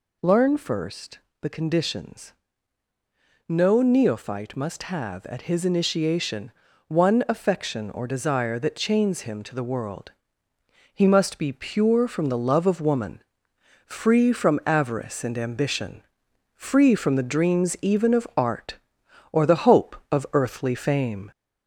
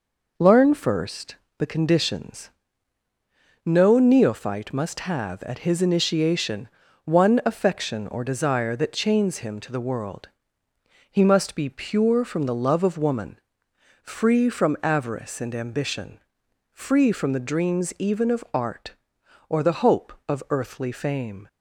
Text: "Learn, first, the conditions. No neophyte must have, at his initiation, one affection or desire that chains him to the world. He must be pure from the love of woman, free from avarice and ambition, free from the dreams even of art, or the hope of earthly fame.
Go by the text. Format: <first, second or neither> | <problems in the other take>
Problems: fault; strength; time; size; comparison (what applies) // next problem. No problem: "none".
second | gets louder; slight; throughout; 2.5 dB